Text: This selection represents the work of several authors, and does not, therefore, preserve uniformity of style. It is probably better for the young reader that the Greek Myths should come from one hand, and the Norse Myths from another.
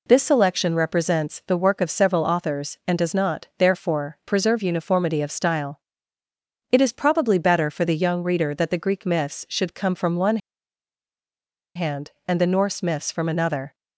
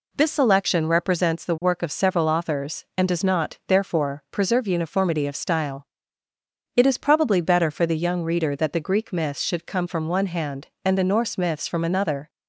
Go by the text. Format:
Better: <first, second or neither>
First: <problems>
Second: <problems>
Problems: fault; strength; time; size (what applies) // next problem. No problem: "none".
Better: second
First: pauses between "one" and "hand"; strong; at 10.3 s; 1.3 s long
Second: none